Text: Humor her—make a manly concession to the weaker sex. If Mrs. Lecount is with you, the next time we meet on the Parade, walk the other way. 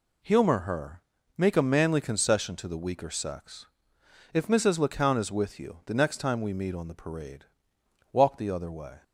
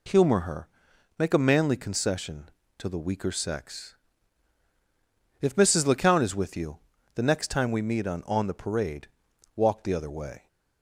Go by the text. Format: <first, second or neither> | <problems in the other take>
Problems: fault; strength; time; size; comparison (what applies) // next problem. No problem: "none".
first | says "on" twice; at 8.2 s